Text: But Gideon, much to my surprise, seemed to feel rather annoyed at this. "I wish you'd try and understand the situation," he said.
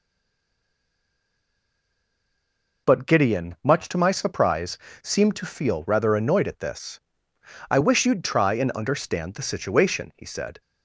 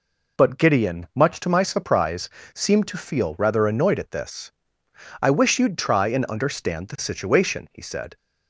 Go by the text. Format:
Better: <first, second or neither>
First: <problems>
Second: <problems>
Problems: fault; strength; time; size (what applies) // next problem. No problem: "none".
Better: second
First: stays silent before the first word; strong; until 2.8 s; 2.8 s long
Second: none